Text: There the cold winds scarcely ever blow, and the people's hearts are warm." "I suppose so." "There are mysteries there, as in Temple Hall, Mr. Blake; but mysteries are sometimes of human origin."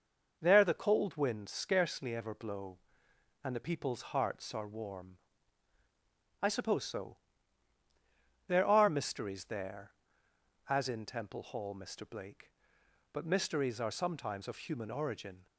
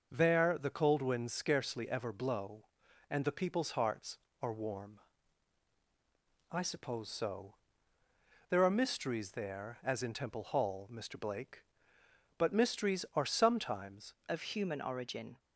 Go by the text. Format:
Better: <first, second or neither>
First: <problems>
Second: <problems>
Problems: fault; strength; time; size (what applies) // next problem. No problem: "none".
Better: first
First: none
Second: changes voice at "of"; from 14.2 s on; 1.1 s long